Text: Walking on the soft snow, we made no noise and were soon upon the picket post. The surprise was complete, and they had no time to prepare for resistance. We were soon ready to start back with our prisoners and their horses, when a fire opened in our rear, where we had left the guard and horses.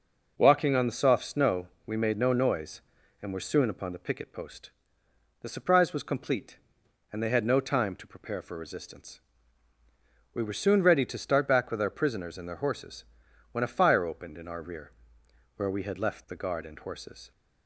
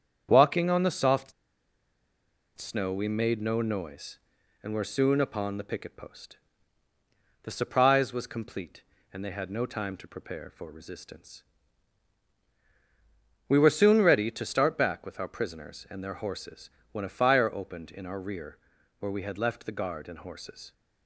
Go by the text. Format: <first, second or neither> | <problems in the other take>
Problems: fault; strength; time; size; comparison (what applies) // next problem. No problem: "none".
first | starts louder than the rest; strong; until 1.3 s; 8 dB // pauses between "soft" and "snow"; strong; at 1.3 s; 1.2 s long